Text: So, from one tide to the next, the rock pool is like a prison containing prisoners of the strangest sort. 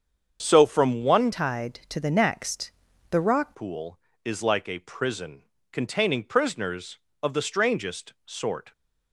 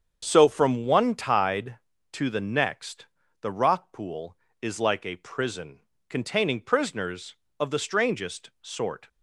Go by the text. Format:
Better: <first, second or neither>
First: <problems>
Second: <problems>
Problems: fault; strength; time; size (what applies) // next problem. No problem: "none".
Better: second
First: starts louder than the rest; strong; until 1.4 s; 7 dB // changes voice from "tide" to "rock"; from 1.3 to 3.5 s; 2.2 s long // pauses between "prison" and "containing"; slight; at 5.4 s; 0.28 s long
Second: starts louder than the rest; strong; until 1.2 s; 7.5 dB // pauses between "prison" and "containing"; slight; at 5.8 s; 0.28 s long